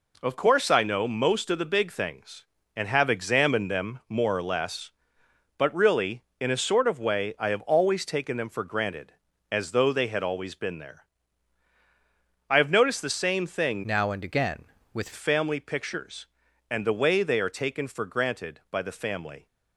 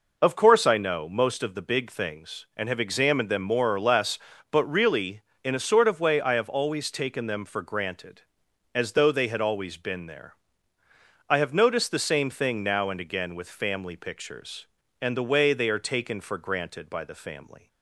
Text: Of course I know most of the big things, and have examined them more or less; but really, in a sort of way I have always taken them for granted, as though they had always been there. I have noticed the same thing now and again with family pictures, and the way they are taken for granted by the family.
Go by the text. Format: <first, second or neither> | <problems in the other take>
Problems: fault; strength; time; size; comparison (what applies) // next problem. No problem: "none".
second | changes voice from "now" to "with"; from 13.8 to 15.0 s; 1.2 s long